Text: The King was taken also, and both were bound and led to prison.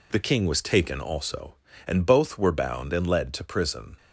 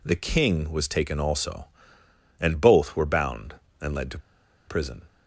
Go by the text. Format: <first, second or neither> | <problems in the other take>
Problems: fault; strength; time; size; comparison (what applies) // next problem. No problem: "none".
first | pauses between "to" and "prison"; noticeable; at 4.1 s; 0.49 s long